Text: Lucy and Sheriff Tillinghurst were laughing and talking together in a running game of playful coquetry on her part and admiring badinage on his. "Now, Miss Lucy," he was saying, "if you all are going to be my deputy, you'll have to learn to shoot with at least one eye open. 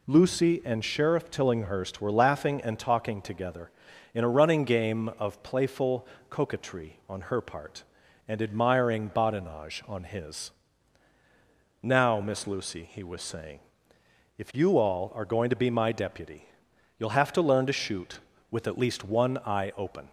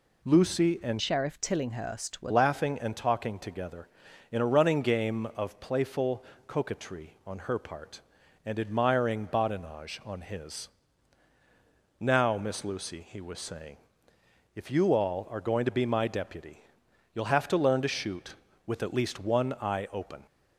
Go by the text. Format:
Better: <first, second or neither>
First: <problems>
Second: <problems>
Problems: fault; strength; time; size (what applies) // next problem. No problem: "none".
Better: first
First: pauses between "playful" and "coquetry"; slight; at 6.0 s; 0.22 s long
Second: changes voice from "Sheriff" to "were"; from 0.9 to 2.3 s; 1.4 s long // pauses between "playful" and "coquetry"; slight; at 6.2 s; 0.22 s long